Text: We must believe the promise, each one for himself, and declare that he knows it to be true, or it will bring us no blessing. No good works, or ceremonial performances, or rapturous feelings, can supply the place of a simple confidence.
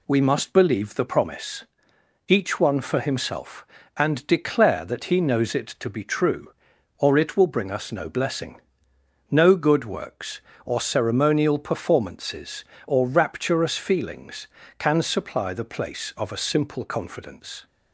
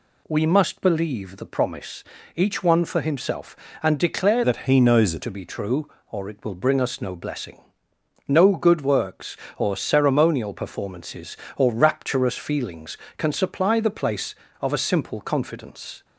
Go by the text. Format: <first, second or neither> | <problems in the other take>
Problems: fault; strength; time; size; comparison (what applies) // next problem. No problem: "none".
first | changes voice from "that" to "it"; from 4.4 to 5.2 s; 0.8 s long